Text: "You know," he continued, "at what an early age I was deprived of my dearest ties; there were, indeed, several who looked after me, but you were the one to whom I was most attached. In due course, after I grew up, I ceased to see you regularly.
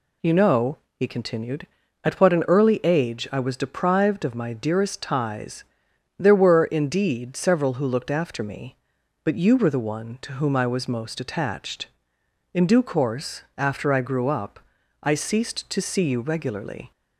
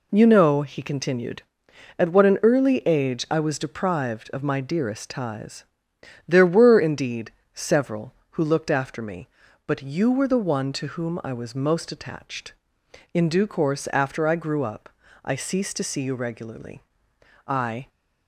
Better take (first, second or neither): first